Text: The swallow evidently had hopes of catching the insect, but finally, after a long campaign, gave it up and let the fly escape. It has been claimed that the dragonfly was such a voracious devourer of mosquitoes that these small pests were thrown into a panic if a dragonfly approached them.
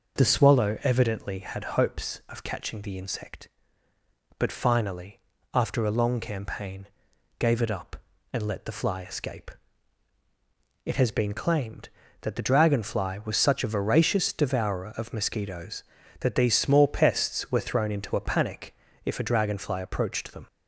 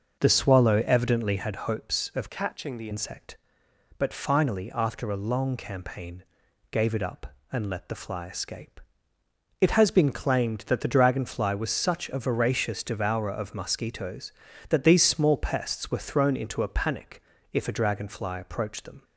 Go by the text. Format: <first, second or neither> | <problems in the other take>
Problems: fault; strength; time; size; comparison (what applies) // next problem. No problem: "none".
first | changes voice from "catching" to "the"; from 2.2 to 2.9 s; 0.7 s long // pauses between "panic" and "if"; slight; at 17.2 s; 0.32 s long; slight in the first